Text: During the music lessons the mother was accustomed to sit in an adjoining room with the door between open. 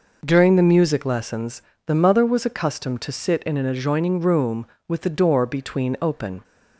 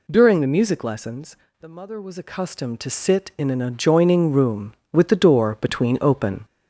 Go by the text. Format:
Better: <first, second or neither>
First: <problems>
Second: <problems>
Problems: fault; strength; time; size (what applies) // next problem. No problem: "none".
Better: first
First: pauses between "lessons" and "the"; slight; at 1.6 s; 0.24 s long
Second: gets louder; throughout; 4 dB // pauses between "lessons" and "the"; slight; at 1.3 s; 0.26 s long